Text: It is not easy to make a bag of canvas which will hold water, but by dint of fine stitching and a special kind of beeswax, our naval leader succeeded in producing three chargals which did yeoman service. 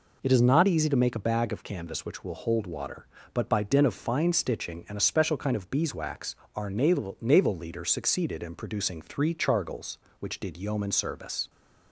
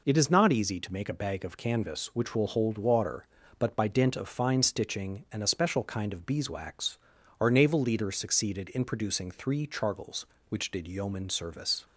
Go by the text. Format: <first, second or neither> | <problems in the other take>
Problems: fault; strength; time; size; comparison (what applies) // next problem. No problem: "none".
second | says "naval" twice; at 7.2 s